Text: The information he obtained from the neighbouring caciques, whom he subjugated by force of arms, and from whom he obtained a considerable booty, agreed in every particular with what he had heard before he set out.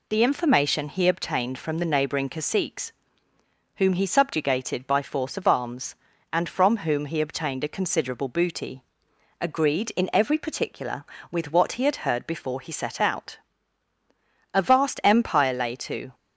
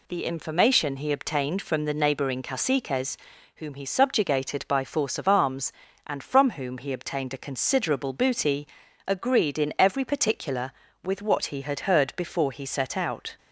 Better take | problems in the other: second | goes on to say "A vast empire lay to"; from 14.5 s on; 1.6 s long

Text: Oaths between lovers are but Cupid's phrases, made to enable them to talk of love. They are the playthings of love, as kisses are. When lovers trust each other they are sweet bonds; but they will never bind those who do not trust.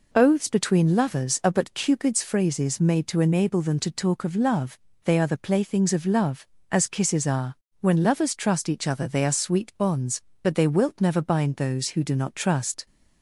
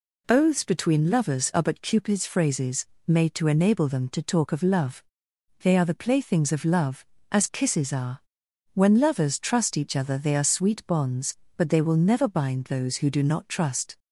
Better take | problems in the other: second | says "wilt" for "will"; at 10.6 s

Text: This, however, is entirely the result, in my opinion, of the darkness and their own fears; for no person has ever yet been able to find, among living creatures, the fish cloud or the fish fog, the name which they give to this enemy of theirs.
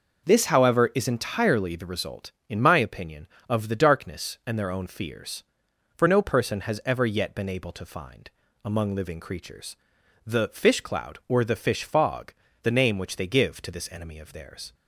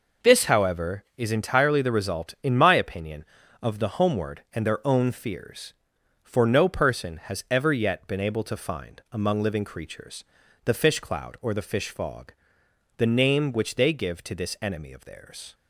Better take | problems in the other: first | says "homeward" for "darkness"; at 3.9 s

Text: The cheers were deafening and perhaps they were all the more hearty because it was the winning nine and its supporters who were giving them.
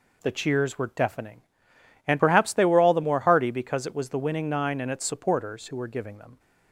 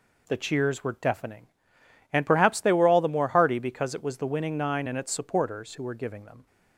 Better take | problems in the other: neither | none

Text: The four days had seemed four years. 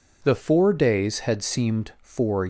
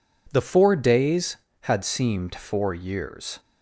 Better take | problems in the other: second | stops before "years"; at 2.4 s

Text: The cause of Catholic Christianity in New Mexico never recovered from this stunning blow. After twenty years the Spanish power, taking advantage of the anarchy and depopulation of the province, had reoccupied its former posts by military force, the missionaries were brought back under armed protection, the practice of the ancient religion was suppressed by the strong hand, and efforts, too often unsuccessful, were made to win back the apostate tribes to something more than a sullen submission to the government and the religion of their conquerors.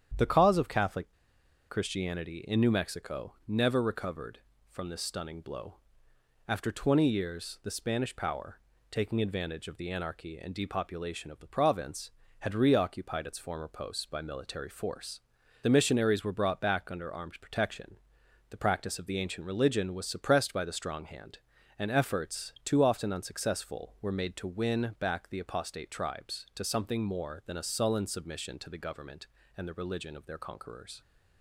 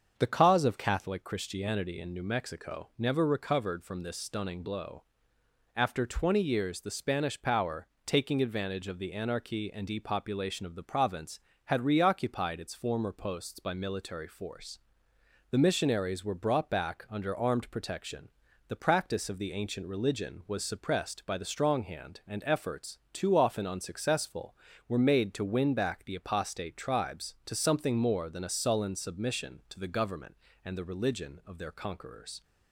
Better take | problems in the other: second | starts louder than the rest; strong; until 1.8 s; 9 dB; also in the second // pauses between "Catholic" and "Christianity"; noticeable; at 1.0 s; 0.62 s long

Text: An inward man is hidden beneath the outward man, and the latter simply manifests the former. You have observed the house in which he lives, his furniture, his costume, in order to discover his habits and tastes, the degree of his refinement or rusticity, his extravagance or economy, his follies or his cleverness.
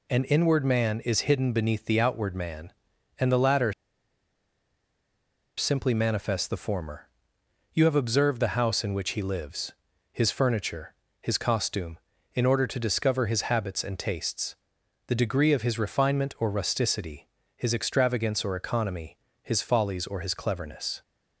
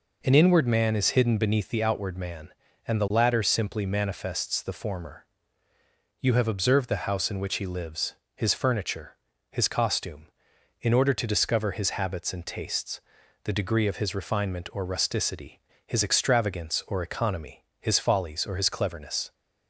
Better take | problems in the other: second | pauses between "latter" and "simply"; strong; at 3.7 s; 1.8 s long

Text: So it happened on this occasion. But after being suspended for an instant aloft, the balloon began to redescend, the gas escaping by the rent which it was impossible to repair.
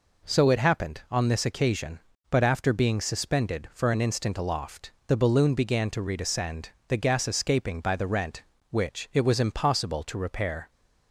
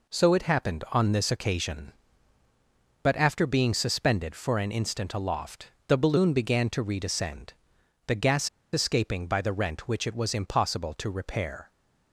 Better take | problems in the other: first | pauses between "gas" and "escaping"; slight; at 8.4 s; 0.24 s long

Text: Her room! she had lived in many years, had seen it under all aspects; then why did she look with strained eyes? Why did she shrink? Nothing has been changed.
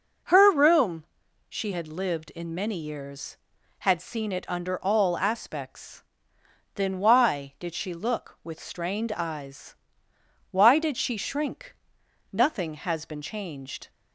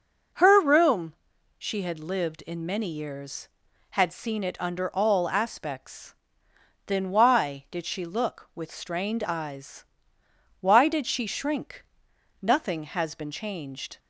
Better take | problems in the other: neither | none

